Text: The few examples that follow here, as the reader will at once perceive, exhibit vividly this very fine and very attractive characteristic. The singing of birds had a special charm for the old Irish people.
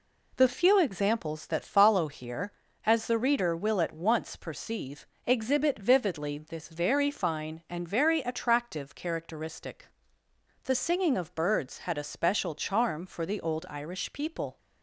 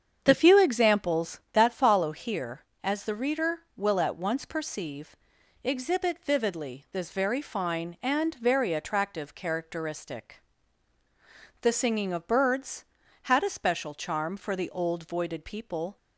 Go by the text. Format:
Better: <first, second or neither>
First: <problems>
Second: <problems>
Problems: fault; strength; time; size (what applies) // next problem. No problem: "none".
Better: first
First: none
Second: starts louder than the rest; strong; until 1.2 s; 7.5 dB // says "Voided" for "Irish"; at 15.0 s